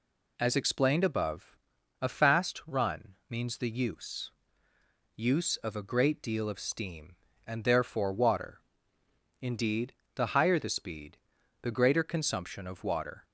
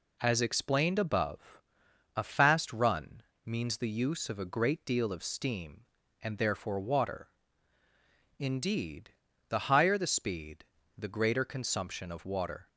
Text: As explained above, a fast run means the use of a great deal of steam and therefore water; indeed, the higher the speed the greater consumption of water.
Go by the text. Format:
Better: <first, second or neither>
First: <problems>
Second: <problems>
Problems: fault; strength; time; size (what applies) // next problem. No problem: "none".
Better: second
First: pauses between "run" and "means"; slight; at 3.1 s; 0.16 s long // says "use" twice; at 5.1 s // pauses between "speed" and "the"; at 11.1 s; 0.42 s long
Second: pauses between "run" and "means"; slight; at 3.2 s; 0.24 s long // pauses between "speed" and "the"; slight; at 10.6 s; 0.34 s long